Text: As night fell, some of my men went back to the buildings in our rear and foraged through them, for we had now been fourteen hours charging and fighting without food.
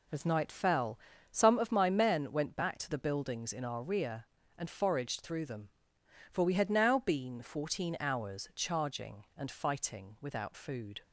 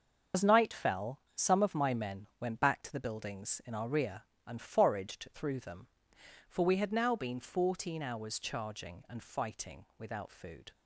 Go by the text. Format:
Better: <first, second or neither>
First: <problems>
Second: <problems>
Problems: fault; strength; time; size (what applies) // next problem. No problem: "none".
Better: first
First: none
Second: loses the start of "As"; at 0.3 s; 65 ms // starts louder than the rest; until 1.5 s; 6 dB